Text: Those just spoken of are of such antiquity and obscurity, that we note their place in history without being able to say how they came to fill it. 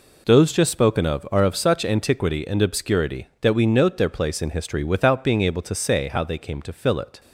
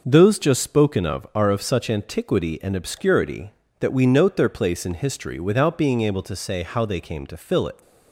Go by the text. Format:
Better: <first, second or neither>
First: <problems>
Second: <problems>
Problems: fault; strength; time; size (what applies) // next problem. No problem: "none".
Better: neither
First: none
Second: none